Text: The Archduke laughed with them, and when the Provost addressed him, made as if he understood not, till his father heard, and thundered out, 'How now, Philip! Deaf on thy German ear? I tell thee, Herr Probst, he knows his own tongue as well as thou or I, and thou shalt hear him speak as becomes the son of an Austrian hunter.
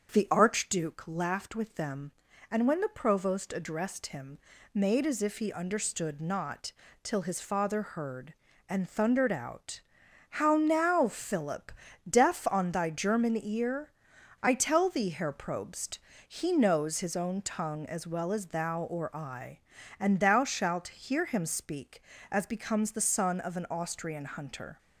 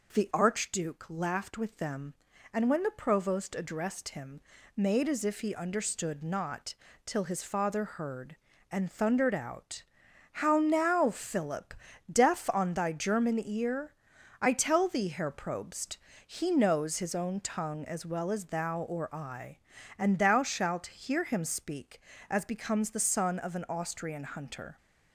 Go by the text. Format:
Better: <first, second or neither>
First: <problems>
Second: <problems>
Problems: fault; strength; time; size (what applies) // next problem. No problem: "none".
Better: second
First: starts louder than the rest; until 1.2 s; 6.5 dB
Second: none